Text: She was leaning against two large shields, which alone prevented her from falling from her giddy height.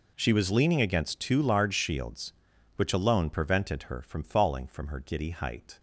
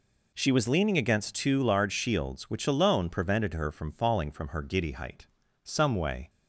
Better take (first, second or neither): first